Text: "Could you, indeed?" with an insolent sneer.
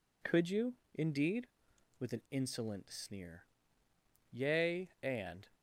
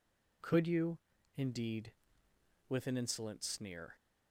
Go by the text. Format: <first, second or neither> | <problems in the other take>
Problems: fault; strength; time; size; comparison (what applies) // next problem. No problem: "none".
second | goes on to say "Yea and"; noticeable; from 4.3 s on; 1.1 s long